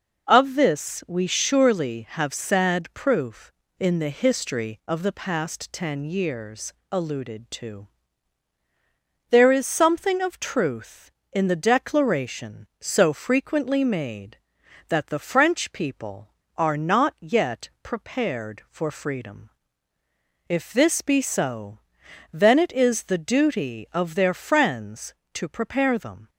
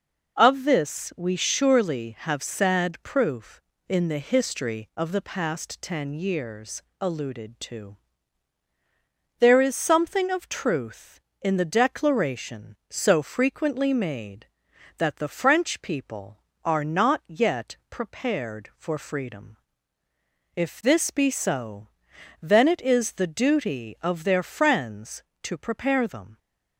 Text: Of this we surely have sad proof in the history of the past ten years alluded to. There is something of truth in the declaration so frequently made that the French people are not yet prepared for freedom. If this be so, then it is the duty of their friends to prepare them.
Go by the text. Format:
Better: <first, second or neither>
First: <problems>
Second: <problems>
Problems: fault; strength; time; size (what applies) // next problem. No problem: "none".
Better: neither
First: pauses between "years" and "alluded"; slight; at 6.7 s; 0.18 s long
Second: pauses between "years" and "alluded"; slight; at 6.8 s; 0.18 s long